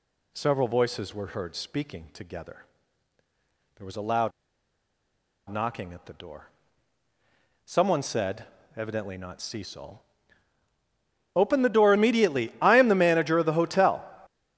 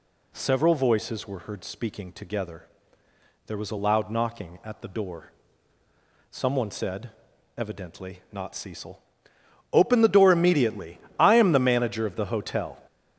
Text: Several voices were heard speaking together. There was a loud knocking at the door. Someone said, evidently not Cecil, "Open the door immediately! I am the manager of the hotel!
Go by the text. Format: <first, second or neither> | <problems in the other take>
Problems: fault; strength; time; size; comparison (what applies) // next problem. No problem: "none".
second | pauses between "loud" and "knocking"; at 4.3 s; 1.1 s long